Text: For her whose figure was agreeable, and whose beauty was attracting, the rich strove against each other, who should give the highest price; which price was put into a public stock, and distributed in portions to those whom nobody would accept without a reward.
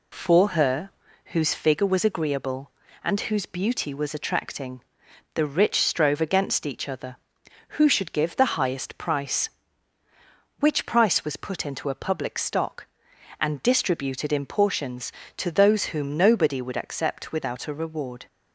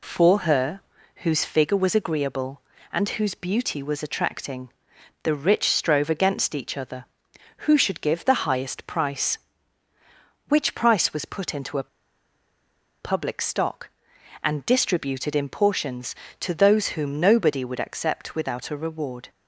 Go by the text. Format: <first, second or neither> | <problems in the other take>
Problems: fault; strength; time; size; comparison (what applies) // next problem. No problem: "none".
first | pauses between "her" and "whose"; at 0.8 s; 0.42 s long; also in the first // pauses between "a" and "public"; at 11.8 s; 1.1 s long